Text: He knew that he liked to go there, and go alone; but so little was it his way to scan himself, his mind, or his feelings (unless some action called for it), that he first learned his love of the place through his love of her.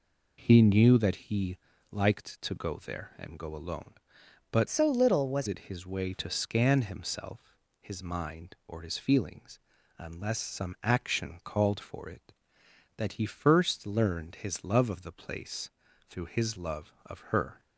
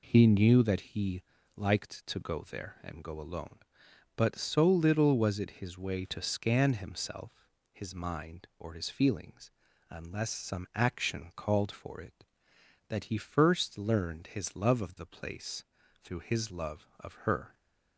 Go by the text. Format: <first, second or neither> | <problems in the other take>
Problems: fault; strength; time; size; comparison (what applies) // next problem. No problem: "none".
second | pauses between "he" and "liked"; slight; at 1.5 s; 0.34 s long; slight in the second // changes voice from "so" to "was"; from 4.6 to 5.4 s; 0.8 s long // pauses between "place" and "through"; at 15.7 s; 0.40 s long; also in the second